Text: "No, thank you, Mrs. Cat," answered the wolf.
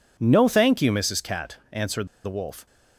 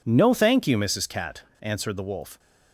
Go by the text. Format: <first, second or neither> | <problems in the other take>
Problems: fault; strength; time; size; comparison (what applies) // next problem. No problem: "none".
second | pauses between "answered" and "the"; slight; at 2.0 s; 0.17 s long